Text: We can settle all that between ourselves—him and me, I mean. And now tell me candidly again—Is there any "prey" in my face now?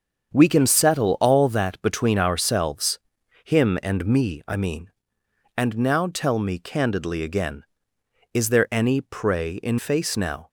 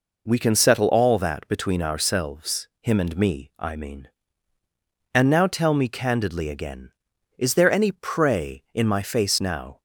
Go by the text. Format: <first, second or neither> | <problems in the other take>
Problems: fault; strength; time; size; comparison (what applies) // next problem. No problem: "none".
second | starts louder than the rest; until 1.3 s; 7 dB // skips "my"; at 9.7 s